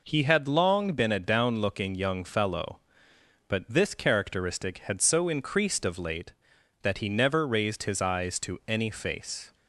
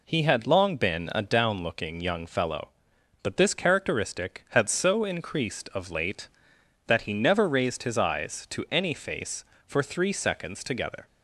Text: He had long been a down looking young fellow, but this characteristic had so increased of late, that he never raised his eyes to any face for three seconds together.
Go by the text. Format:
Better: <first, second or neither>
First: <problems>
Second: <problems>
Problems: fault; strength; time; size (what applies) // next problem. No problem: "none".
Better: second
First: stops before "for three seconds together"; at 9.5 s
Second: none